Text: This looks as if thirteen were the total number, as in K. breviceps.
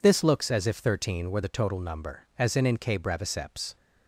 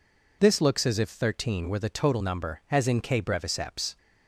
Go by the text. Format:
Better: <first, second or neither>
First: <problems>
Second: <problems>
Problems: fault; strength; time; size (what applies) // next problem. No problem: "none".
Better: second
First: says "in" twice; at 2.6 s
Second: none